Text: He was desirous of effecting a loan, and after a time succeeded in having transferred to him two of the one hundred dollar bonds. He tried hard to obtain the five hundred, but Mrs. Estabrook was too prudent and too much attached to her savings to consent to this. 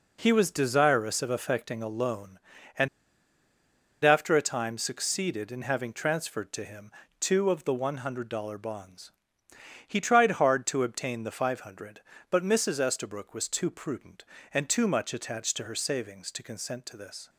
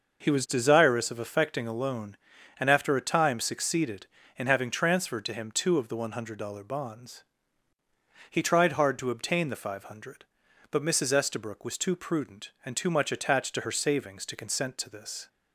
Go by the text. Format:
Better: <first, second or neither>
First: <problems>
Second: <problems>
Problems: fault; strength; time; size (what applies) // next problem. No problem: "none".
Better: second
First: pauses between "and" and "after"; at 2.8 s; 1.1 s long // pauses between "him" and "two"; slight; at 6.9 s; 0.28 s long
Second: none